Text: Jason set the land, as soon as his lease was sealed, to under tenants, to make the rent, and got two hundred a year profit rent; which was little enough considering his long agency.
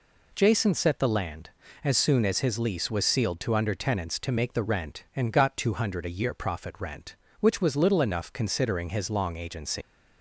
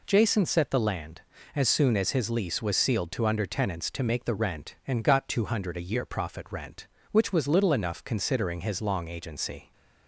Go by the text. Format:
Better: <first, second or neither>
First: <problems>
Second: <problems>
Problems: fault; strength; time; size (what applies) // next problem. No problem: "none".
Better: second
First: leaves "agency" unfinished; at 9.8 s; 190 ms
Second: none